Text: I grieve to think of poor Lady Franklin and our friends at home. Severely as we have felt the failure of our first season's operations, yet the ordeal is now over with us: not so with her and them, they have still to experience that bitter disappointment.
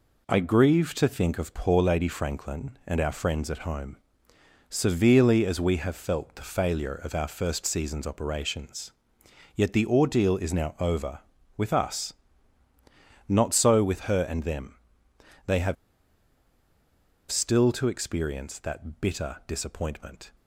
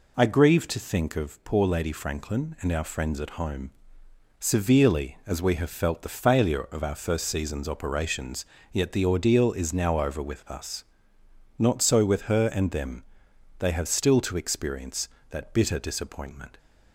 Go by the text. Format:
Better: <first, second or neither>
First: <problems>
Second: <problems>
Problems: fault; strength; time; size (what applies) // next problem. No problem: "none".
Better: second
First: pauses between "have" and "still"; strong; at 15.7 s; 1.5 s long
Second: none